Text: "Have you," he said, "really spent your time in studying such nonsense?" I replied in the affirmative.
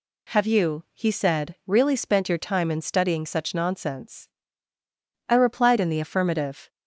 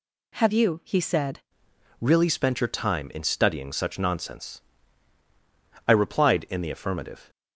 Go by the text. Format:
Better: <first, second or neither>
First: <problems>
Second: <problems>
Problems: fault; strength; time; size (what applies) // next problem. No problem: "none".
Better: first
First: none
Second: changes voice at "really"; from 1.9 s on; 5.3 s long